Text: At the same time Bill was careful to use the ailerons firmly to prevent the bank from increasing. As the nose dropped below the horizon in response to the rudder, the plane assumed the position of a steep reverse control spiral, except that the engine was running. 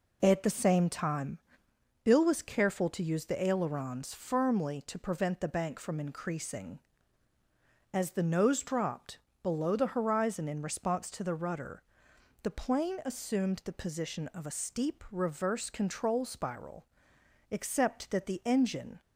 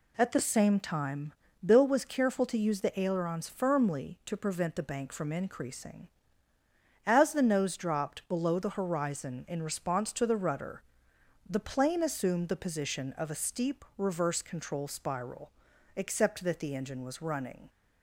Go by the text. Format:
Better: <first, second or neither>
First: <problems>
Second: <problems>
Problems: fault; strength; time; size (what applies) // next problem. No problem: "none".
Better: second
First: pauses between "time" and "Bill"; noticeable; at 1.3 s; 0.64 s long // pauses between "dropped" and "below"; slight; at 9.1 s; 0.24 s long // stops before "was running"; at 19.0 s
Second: pauses between "time" and "Bill"; slight; at 1.3 s; 0.30 s long